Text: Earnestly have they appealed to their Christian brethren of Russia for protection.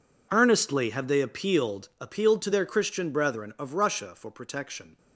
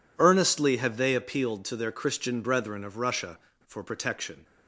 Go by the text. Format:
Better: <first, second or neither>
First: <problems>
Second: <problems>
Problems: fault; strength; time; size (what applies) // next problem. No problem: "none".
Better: second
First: says "appealed" twice; at 1.9 s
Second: none